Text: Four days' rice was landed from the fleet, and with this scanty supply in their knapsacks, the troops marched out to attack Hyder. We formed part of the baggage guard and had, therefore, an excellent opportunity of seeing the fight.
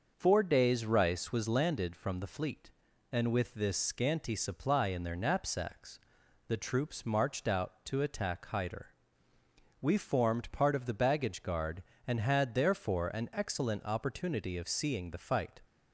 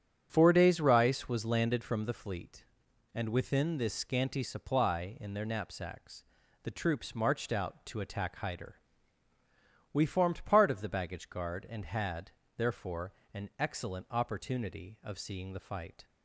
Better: first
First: starts louder than the rest; until 1.1 s; 6 dB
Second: starts louder than the rest; strong; until 1.3 s; 8.5 dB // says "within" for "with"; at 3.2 s

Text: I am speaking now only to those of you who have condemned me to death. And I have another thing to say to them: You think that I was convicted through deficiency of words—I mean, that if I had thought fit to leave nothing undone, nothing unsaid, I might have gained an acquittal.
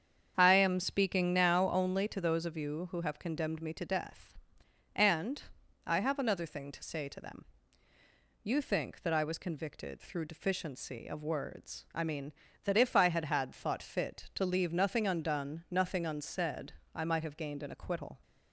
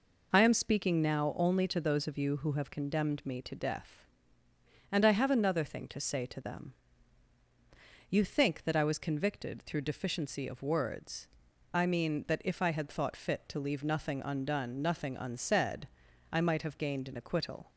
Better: second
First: starts louder than the rest; strong; until 1.3 s; 7.5 dB // pauses between "And" and "I"; noticeable; at 5.4 s; 0.46 s long // says "had" twice; at 13.2 s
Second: none

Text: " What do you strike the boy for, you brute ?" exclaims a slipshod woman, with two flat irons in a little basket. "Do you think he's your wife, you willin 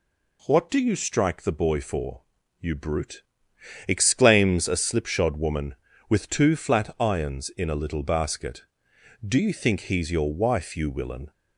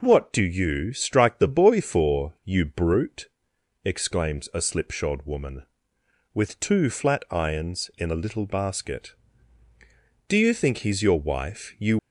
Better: first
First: none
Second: stops before "willin"; at 11.9 s

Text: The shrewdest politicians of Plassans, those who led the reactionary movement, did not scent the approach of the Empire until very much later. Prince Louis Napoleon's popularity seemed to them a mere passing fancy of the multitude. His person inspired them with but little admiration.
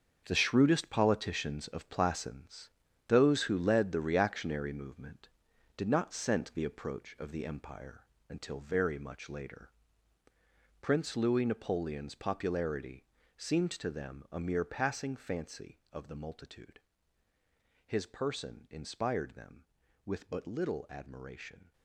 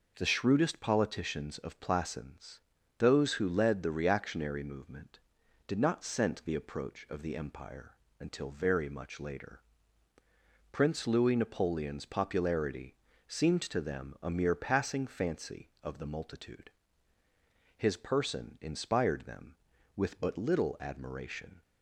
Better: second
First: gets quieter; strong; throughout; 11 dB // pauses between "Empire" and "until"; slight; at 8.0 s; 0.22 s long // pauses between "popularity" and "seemed"; slight; at 13.0 s; 0.32 s long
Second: pauses between "Empire" and "until"; slight; at 7.9 s; 0.22 s long // pauses between "popularity" and "seemed"; slight; at 12.9 s; 0.32 s long

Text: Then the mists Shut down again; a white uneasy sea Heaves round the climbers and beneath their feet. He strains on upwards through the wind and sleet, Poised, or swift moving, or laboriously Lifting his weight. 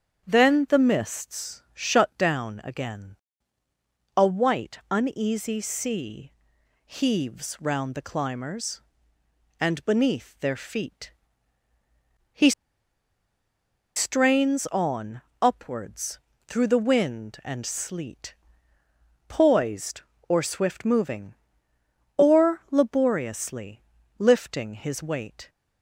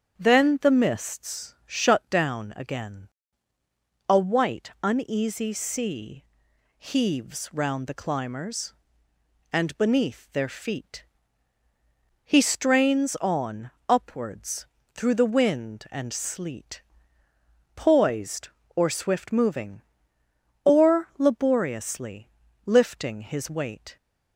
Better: second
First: starts louder than the rest; strong; until 1.3 s; 7.5 dB // pauses between "sea" and "Heaves"; noticeable; at 6.3 s; 0.54 s long // pauses between "He" and "strains"; strong; at 12.5 s; 1.4 s long // pauses between "on" and "upwards"; slight; at 15.2 s; 0.20 s long // pauses between "upwards" and "through"; slight; at 16.1 s; 0.28 s long // pauses between "laboriously" and "Lifting"; slight; at 23.8 s; 0.36 s long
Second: starts louder than the rest; strong; until 1.2 s; 7.5 dB // pauses between "sea" and "Heaves"; noticeable; at 6.2 s; 0.54 s long // pauses between "on" and "upwards"; slight; at 13.7 s; 0.18 s long // pauses between "upwards" and "through"; slight; at 14.6 s; 0.28 s long // pauses between "laboriously" and "Lifting"; slight; at 22.2 s; 0.36 s long

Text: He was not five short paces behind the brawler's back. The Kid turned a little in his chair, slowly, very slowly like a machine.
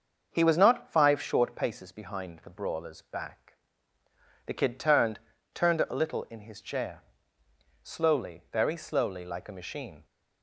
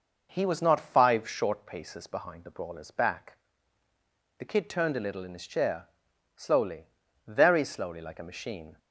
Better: second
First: starts louder than the rest; until 1.3 s; 6.5 dB // says "turned" twice; at 5.5 s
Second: none

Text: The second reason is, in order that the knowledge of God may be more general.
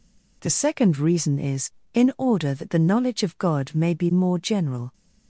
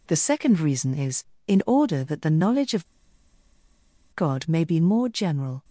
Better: first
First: none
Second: pauses between "of" and "God"; strong; at 2.8 s; 1.3 s long

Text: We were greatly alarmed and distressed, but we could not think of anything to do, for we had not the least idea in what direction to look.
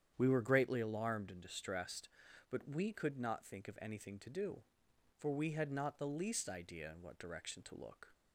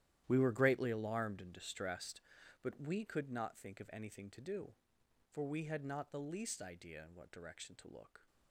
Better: first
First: starts louder than the rest; strong; until 1.1 s; 9 dB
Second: gets quieter; strong; throughout; 14 dB // starts louder than the rest; strong; until 1.2 s; 12 dB

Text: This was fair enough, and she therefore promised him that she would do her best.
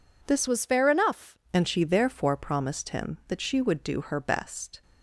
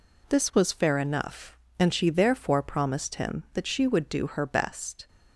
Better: second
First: changes voice from "was" to "enough"; from 0.4 to 1.3 s; 0.9 s long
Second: none

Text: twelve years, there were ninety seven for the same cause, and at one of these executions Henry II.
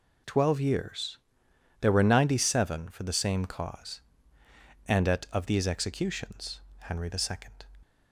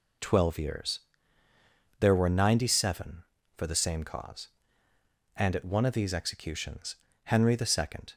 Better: second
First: skips "one"; at 5.2 s // pauses between "executions" and "Henry"; slight; at 6.5 s; 0.20 s long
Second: pauses between "executions" and "Henry"; slight; at 6.9 s; 0.30 s long

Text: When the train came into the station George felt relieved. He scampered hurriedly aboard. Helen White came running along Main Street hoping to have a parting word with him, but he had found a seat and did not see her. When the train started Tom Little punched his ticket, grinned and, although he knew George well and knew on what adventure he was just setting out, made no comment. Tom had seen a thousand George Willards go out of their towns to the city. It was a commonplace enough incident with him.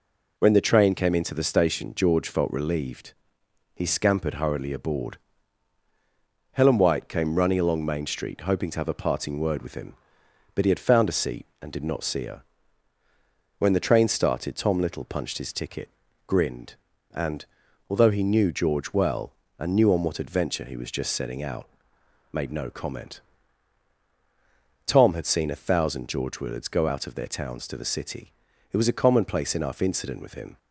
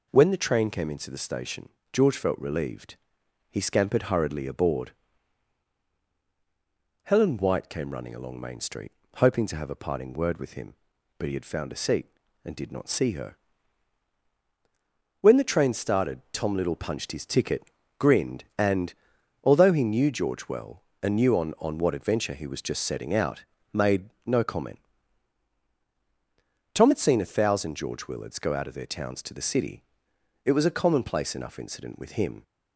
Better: first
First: none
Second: pauses between "station" and "George"; slight; at 1.6 s; 0.22 s long // pauses between "Street" and "hoping"; slight; at 8.9 s; 0.24 s long // says "on" twice; at 21.5 s // pauses between "made" and "no"; slight; at 24.0 s; 0.16 s long

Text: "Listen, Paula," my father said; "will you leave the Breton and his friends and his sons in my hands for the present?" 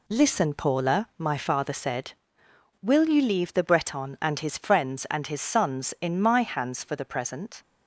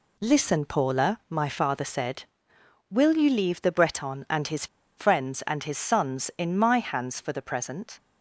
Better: first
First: none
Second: pauses between "his" and "friends"; slight; at 4.6 s; 0.31 s long

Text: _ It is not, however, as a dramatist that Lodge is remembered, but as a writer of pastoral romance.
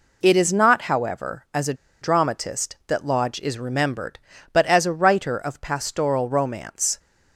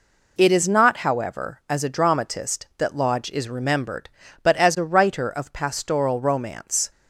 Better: second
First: pauses between "a" and "dramatist"; slight; at 1.7 s; 0.27 s long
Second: none

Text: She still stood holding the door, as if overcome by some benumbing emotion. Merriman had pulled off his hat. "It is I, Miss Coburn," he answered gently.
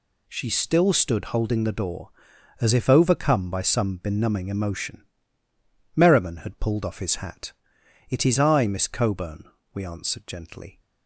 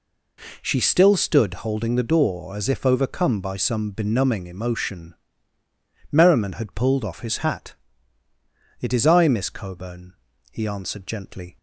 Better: second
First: says "we" for "he"; at 9.7 s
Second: none

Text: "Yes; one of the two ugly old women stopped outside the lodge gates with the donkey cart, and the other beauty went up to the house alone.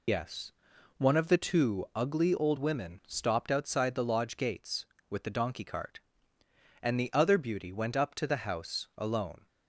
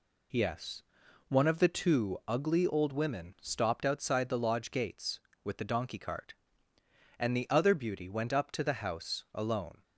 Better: second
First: loses the start of "Yes"; at 0.0 s; 65 ms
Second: none

